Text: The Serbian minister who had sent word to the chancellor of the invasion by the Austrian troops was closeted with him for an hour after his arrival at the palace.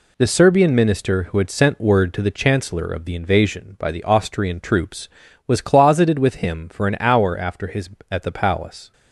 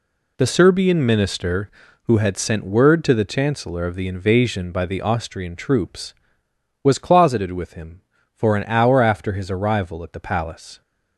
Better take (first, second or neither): second